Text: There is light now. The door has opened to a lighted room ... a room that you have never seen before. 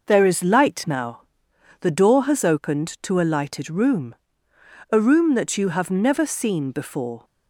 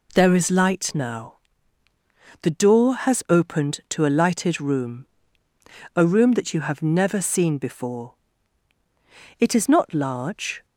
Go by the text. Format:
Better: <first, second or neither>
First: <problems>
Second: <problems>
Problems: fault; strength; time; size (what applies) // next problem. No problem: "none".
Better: first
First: none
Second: goes on to say "It is not large"; noticeable; from 9.3 s on; 1.2 s long